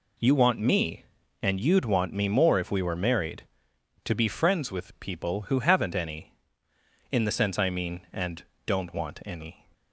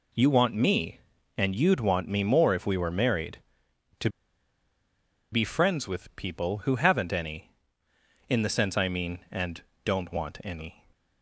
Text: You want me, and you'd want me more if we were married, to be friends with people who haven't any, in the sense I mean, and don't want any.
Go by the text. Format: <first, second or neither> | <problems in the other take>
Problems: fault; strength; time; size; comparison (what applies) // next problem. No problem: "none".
first | pauses between "to" and "be"; at 4.1 s; 1.2 s long // pauses between "and" and "don't"; slight; at 9.6 s; 0.22 s long; slight in the first